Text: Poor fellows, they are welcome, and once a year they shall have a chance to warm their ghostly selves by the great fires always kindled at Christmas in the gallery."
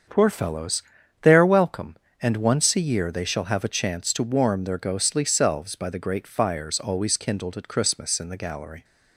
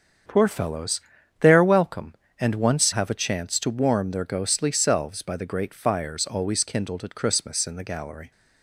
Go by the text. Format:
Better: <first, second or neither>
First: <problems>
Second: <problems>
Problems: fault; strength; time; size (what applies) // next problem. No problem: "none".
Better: first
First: starts louder than the rest; until 1.4 s; 7 dB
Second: starts louder than the rest; strong; until 1.6 s; 7.5 dB // skips "a year they shall"; at 2.9 s